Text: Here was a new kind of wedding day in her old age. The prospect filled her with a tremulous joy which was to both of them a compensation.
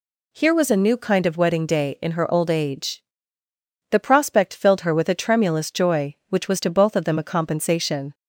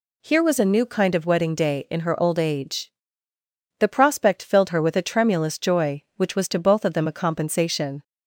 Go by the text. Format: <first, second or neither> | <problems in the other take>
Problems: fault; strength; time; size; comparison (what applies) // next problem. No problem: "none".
neither | none